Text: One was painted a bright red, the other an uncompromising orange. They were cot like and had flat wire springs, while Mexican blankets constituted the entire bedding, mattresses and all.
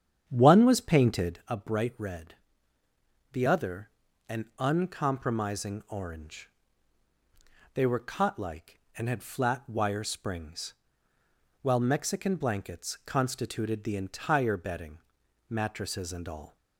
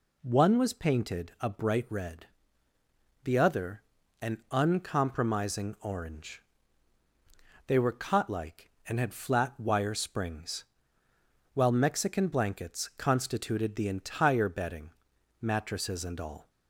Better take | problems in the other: second | starts louder than the rest; strong; until 1.5 s; 9 dB // pauses between "other" and "an"; at 3.8 s; 0.38 s long; also in the second

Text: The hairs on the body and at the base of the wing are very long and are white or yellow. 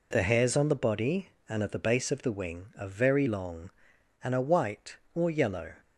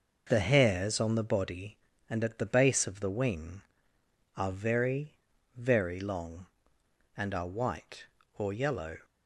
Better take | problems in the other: first | says "very" twice; at 5.5 s

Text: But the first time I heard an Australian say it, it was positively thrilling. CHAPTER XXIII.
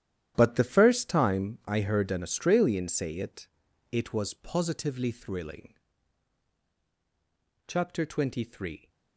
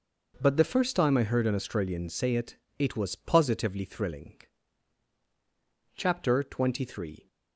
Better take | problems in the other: second | gets quieter; strong; throughout; 13.5 dB

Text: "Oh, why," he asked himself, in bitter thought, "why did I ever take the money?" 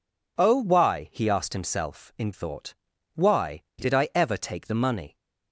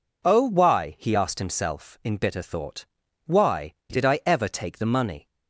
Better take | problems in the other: second | skips "bitter"; at 2.3 s

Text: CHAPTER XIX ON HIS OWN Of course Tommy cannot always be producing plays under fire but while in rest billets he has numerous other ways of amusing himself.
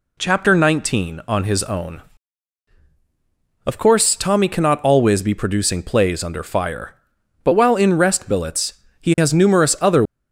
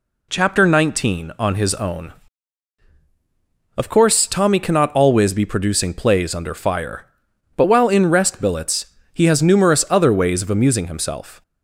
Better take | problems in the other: second | pauses between "billets" and "he"; slight; at 8.7 s; 0.20 s long; slight in the second // stops before "ways of amusing himself"; at 10.0 s

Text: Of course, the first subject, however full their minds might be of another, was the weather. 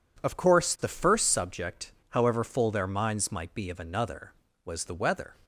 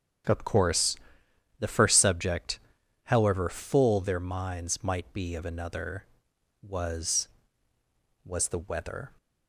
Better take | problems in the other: first | starts louder than the rest; strong; until 1.9 s; 8.5 dB // says "was" twice; at 8.2 s

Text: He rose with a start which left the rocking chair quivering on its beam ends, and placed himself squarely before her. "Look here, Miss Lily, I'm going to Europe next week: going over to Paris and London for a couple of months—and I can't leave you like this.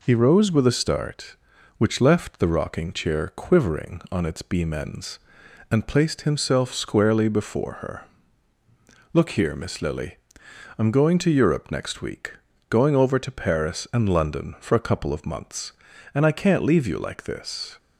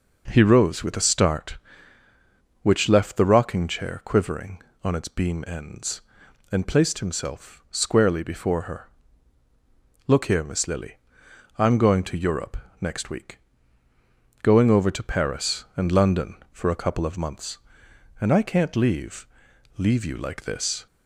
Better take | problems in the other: first | pauses between "Europe" and "next"; slight; at 12.5 s; 0.24 s long // says "leave" twice; at 19.7 s

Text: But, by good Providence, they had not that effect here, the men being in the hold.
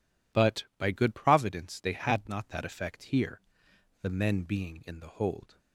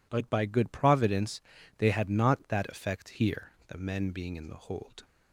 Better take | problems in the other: neither | none

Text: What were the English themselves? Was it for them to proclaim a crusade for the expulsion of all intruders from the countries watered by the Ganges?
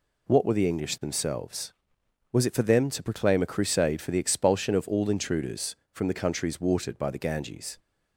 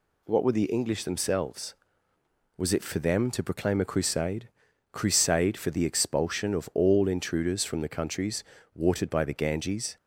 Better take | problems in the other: first | says "crusade" twice; at 4.9 s // pauses between "countries" and "watered"; slight; at 8.4 s; 0.32 s long

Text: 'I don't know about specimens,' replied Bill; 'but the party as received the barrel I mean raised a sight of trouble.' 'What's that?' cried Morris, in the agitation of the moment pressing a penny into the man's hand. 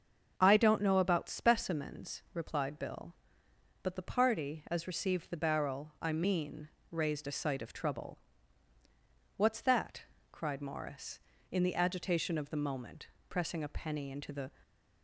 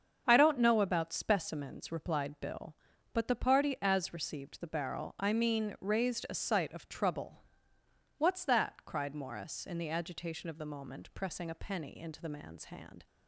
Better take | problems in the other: second | starts louder than the rest; until 1.3 s; 6.5 dB; also in the second // pauses between "mean" and "raised"; slight; at 6.6 s; 0.24 s long // pauses between "moment" and "pressing"; slight; at 13.0 s; 0.22 s long // stops before "man's hand"; at 14.6 s

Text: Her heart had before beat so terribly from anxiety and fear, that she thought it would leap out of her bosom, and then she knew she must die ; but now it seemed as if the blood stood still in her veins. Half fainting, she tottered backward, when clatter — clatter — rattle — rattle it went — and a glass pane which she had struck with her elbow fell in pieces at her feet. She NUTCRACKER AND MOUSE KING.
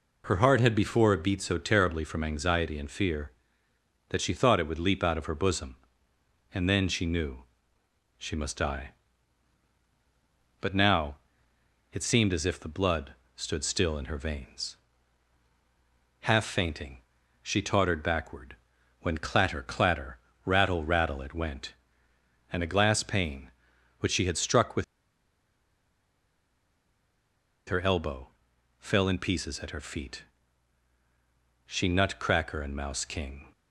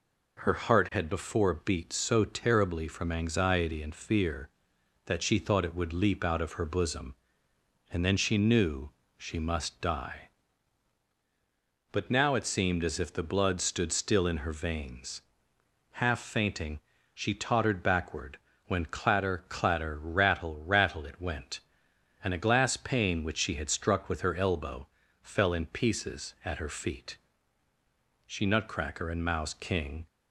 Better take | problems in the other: second | pauses between "knew" and "she"; noticeable; at 7.4 s; 0.74 s long; slight in the second // pauses between "now" and "it"; noticeable; at 11.1 s; 0.76 s long // pauses between "blood" and "stood"; slight; at 13.1 s; 0.22 s long // pauses between "with" and "her"; strong; at 24.8 s; 2.8 s long // pauses between "elbow" and "fell"; noticeable; at 28.2 s; 0.52 s long; slight in the second

